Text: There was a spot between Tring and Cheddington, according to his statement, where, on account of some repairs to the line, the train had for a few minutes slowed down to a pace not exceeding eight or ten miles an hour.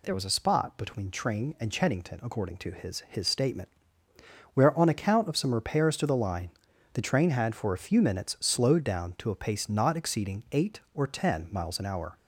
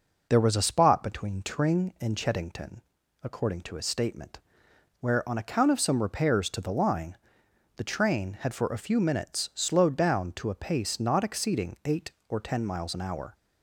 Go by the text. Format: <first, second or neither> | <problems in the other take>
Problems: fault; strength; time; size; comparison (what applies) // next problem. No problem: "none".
second | says "his" twice; at 3.0 s